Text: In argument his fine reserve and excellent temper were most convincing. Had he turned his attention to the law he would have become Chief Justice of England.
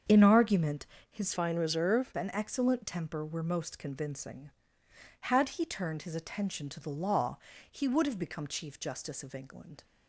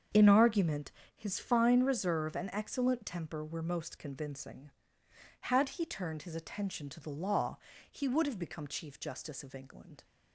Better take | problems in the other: second | starts louder than the rest; strong; until 1.3 s; 7 dB; strong in the second // pauses between "argument" and "his"; slight; at 0.8 s; 0.26 s long; slight in the second // changes voice from "fine" to "reserve"; from 1.3 to 2.1 s; 0.8 s long // pauses between "law" and "he"; slight; at 7.3 s; 0.34 s long; slight in the second

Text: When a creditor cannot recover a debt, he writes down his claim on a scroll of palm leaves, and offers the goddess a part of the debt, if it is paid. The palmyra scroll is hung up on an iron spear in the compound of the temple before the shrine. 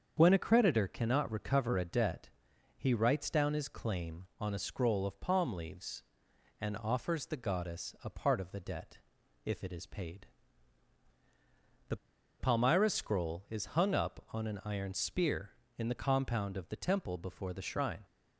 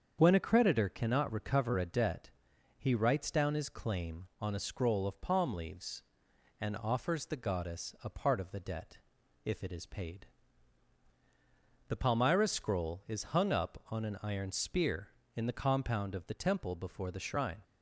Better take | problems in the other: second | starts louder than the rest; strong; until 1.1 s; 7 dB; strong in the second // pauses between "The" and "palmyra"; at 11.9 s; 0.43 s long

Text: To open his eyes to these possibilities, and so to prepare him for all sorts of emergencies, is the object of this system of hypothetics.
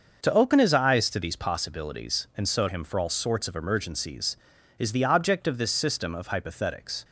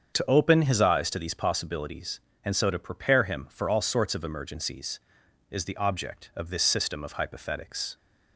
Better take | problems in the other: second | starts louder than the rest; until 1.2 s; 6.5 dB; strong in the second // skips "to prepare"; at 2.6 s

